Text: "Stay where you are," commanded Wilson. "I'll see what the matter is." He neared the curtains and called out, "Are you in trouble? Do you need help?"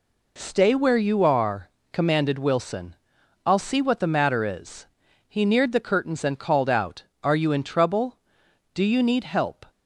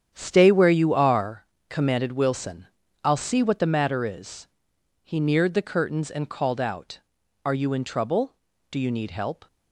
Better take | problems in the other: first | gets quieter; strong; throughout; 11.5 dB

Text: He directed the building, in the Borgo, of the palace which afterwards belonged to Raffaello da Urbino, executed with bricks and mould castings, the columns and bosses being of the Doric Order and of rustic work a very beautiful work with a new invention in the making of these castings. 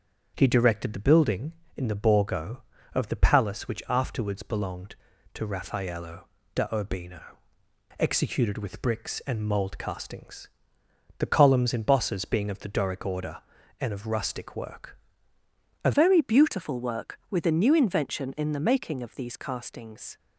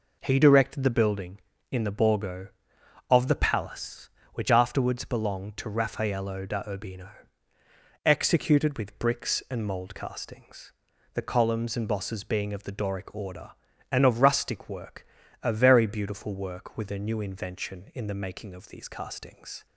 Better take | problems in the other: second | starts louder than the rest; strong; until 1.3 s; 7 dB // pauses between "Raffaello" and "da"; slight; at 6.2 s; 0.28 s long // pauses between "work" and "a"; noticeable; at 14.9 s; 0.86 s long; slight in the second // changes voice at "very"; from 15.9 s on; 4.2 s long

